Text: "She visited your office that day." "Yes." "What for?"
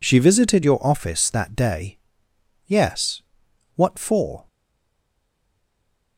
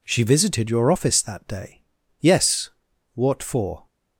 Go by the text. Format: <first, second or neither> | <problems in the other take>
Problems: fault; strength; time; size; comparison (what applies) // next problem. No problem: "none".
second | stays silent after the last word; noticeable; from 4.4 s on; 1.7 s long